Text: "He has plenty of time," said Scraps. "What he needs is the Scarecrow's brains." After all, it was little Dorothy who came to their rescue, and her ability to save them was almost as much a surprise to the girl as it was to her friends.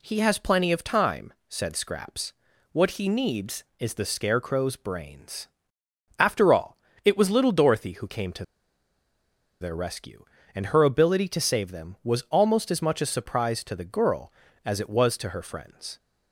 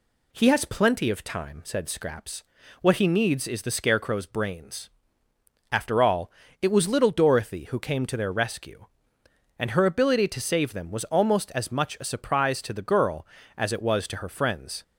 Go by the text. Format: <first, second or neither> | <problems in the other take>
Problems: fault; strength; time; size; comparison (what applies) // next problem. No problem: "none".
second | pauses between "to" and "their"; at 8.4 s; 1.1 s long